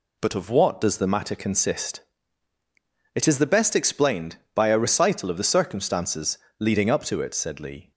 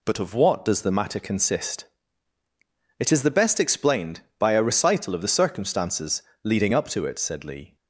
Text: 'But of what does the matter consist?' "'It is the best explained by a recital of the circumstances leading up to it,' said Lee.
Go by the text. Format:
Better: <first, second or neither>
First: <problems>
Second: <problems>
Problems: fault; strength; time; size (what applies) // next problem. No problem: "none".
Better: neither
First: pauses between "circumstances" and "leading"; slight; at 6.3 s; 0.22 s long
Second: pauses between "circumstances" and "leading"; slight; at 6.2 s; 0.22 s long